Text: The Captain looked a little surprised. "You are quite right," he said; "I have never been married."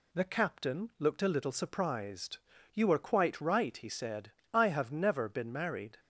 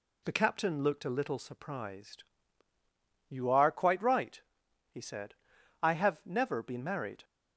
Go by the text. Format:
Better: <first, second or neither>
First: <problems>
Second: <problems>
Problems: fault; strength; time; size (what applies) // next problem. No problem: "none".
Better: neither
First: none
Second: none